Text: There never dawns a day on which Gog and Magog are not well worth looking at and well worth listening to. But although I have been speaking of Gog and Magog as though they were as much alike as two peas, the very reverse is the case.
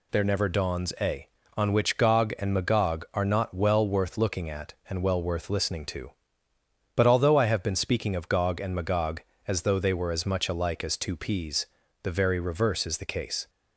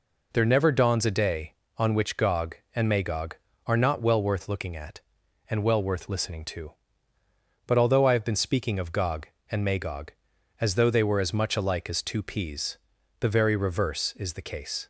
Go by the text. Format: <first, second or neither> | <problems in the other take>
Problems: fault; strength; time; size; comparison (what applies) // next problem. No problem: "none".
second | skips "day"; at 1.4 s